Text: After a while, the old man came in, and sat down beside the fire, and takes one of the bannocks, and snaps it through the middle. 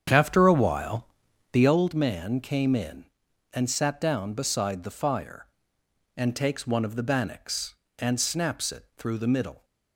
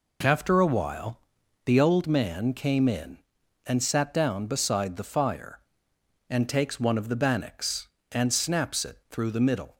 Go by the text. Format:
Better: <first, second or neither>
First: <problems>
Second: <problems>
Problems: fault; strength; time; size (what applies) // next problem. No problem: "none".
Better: second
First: starts louder than the rest; strong; until 1.8 s; 8 dB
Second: none